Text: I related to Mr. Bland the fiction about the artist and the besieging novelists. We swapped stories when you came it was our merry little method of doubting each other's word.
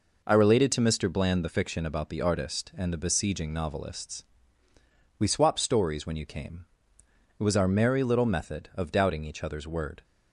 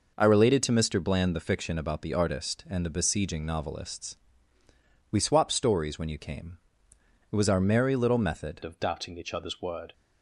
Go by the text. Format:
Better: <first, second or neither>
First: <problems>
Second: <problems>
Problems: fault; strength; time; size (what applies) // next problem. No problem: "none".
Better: first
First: pauses between "came" and "it"; noticeable; at 6.6 s; 0.74 s long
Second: pauses between "came" and "it"; noticeable; at 6.5 s; 0.74 s long // changes voice at "of"; from 8.6 s on; 1.3 s long